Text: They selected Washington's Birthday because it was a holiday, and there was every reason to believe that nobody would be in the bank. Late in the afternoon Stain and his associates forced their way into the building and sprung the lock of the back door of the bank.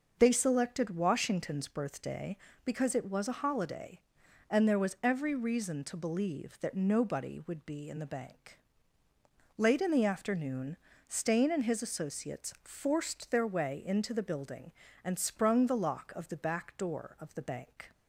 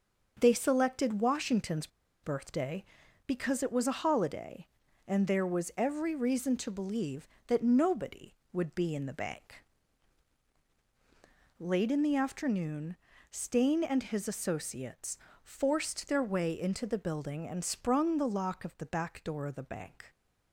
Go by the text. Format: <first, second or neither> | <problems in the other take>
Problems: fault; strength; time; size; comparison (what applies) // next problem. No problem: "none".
first | starts louder than the rest; until 1.4 s; 6.5 dB // pauses between "Washington's" and "Birthday"; slight; at 1.8 s; 0.35 s long // pauses between "afternoon" and "Stain"; slight; at 12.9 s; 0.36 s long; slight in the first // pauses between "associates" and "forced"; slight; at 15.1 s; 0.28 s long